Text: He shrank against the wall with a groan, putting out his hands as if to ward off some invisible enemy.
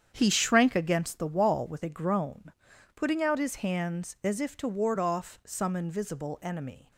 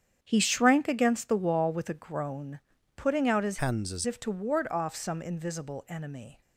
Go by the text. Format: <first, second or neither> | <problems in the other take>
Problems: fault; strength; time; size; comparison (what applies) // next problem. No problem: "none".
first | starts louder than the rest; strong; until 1.2 s; 8.5 dB; strong in the first // changes voice from "hands" to "as"; from 3.5 to 4.0 s; 0.5 s long